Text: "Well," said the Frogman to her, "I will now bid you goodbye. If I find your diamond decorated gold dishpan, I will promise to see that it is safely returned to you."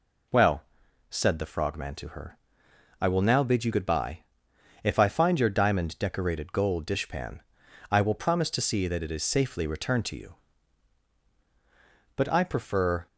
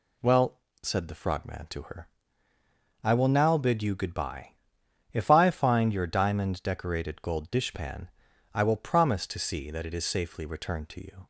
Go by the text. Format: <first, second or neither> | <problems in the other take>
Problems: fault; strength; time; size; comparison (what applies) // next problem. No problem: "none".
second | goes on to say "But I prefer"; noticeable; from 12.1 s on; 0.90 s long